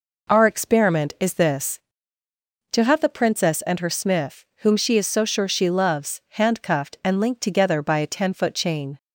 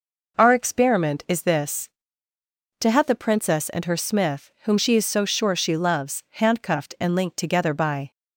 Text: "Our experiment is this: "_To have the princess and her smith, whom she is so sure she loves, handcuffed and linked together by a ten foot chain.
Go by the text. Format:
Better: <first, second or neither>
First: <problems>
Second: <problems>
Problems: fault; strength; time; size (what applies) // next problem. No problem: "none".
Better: first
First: none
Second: stops before "a ten foot chain"; at 8.1 s